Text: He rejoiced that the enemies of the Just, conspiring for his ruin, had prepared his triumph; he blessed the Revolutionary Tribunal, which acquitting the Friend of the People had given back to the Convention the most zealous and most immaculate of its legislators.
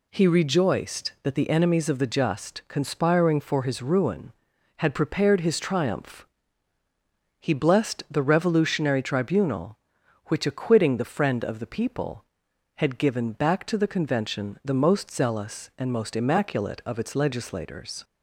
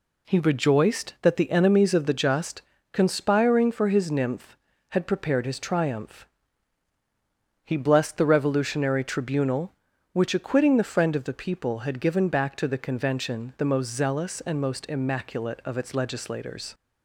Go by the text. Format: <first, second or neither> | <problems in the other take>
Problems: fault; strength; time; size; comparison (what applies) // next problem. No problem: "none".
first | says "nymph" for "ruin"; at 4.0 s